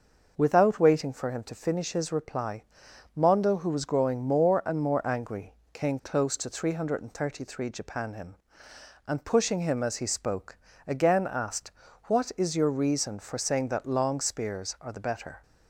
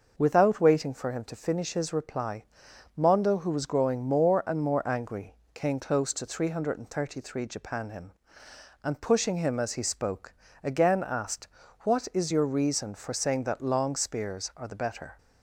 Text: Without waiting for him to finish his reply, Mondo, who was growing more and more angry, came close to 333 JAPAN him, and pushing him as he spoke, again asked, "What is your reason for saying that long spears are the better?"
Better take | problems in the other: neither | none

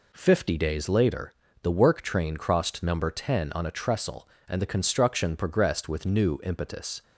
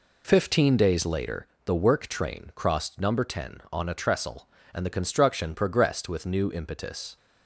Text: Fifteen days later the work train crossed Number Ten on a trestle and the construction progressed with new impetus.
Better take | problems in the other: second | says "Fifty" for "Fifteen"; at 0.1 s // pauses between "later" and "the"; slight; at 1.3 s; 0.28 s long; slight in the second

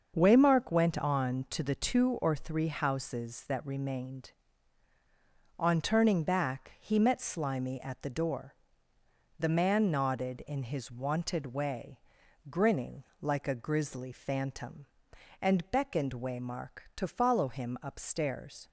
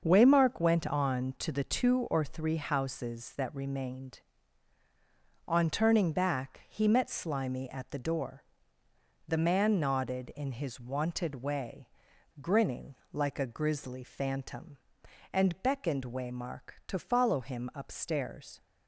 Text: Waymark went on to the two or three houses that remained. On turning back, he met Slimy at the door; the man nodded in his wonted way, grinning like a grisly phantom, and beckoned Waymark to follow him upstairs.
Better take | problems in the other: neither | starts louder than the rest; the same in both // pauses between "grinning" and "like"; slight; the same in both

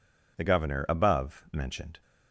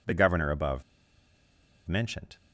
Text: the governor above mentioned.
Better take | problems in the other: first | pauses between "above" and "mentioned"; at 0.8 s; 1.0 s long

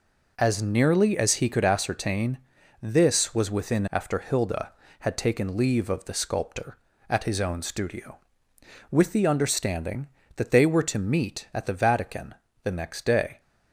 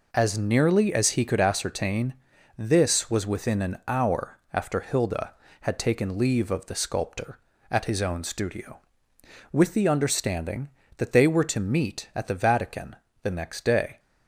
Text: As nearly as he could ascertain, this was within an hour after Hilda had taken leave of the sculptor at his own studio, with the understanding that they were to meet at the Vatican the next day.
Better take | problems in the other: second | skips "an hour"; at 3.8 s // pauses between "Vatican" and "the"; slight; at 12.3 s; 0.28 s long; slight in the second

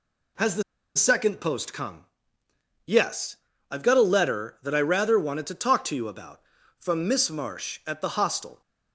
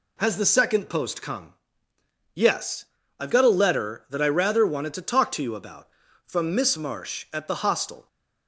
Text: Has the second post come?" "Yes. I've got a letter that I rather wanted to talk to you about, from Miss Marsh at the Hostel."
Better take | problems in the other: second | pauses between "the" and "second"; slight; at 0.6 s; 0.34 s long

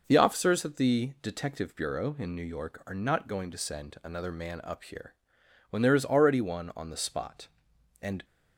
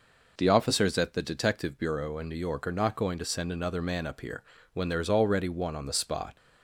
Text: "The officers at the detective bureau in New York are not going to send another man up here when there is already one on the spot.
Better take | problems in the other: second | pauses between "here" and "when"; noticeable; at 5.1 s; 0.56 s long; slight in the second // goes on to say "And"; slight; from 8.0 s on; 0.22 s long

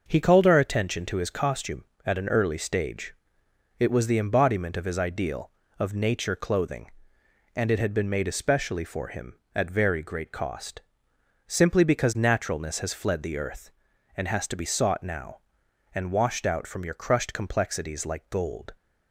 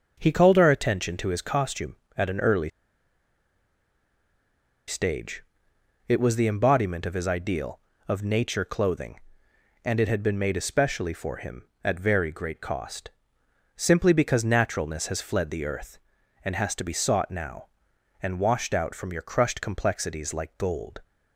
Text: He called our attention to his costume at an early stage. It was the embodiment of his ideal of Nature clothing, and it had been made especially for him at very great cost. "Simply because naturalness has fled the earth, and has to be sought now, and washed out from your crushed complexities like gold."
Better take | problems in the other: first | starts louder than the rest; noticeable; until 1.2 s; 6 dB; noticeable in the first // pauses between "early" and "stage"; strong; at 2.6 s; 2.1 s long

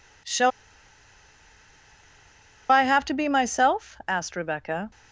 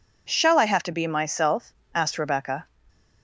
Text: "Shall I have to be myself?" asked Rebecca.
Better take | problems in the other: second | pauses between "Shall" and "I"; strong; at 0.5 s; 2.2 s long

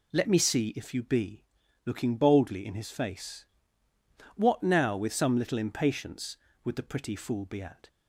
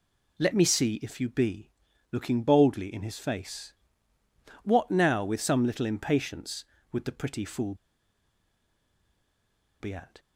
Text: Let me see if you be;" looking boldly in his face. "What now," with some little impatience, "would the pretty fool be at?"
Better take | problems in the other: first | pauses between "fool" and "be"; strong; at 7.7 s; 2.0 s long

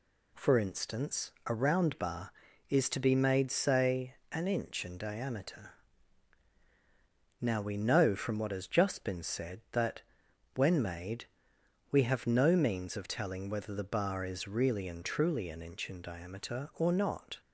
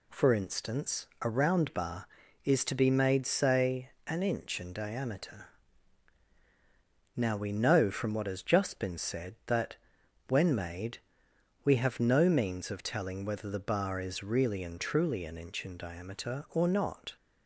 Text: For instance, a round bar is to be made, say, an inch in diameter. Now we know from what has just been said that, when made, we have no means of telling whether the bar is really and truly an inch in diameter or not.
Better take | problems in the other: neither | none

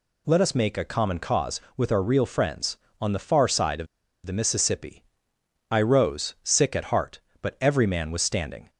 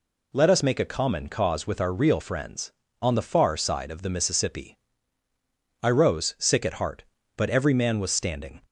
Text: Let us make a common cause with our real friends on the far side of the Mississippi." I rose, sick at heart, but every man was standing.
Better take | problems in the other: second | pauses between "of" and "the"; at 3.8 s; 0.41 s long

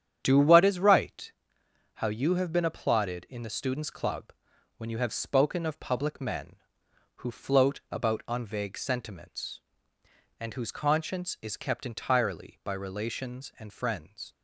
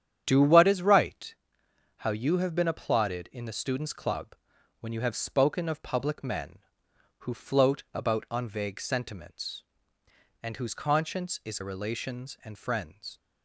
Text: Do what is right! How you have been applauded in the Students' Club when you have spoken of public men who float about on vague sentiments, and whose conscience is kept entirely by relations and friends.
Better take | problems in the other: first | starts louder than the rest; strong; until 1.2 s; 9 dB; strong in the first // pauses between "Club" and "when"; noticeable; at 4.3 s; 0.46 s long; noticeable in the first // skips "kept entirely by"; at 11.5 s

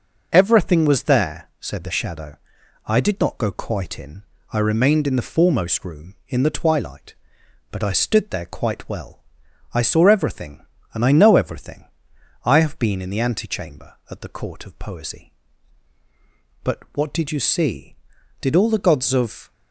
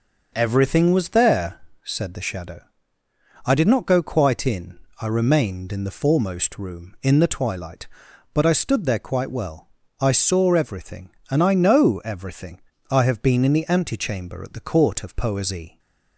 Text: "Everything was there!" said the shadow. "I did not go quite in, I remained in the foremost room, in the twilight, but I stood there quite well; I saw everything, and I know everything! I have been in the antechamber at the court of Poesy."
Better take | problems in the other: second | goes on to say "But WHAT DID you see Did all the gods of"; strong; from 16.6 s on; 2.8 s long

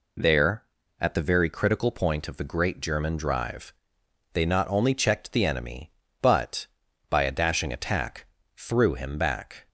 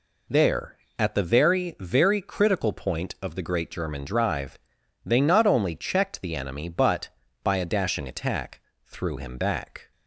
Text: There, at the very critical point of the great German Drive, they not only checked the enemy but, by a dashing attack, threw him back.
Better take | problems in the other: first | says "very" twice; at 1.7 s

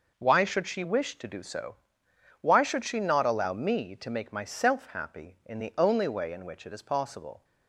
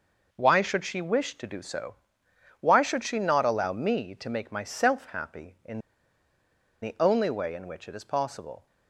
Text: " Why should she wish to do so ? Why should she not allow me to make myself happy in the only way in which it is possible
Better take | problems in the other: first | pauses between "in" and "the"; at 5.8 s; 1.0 s long

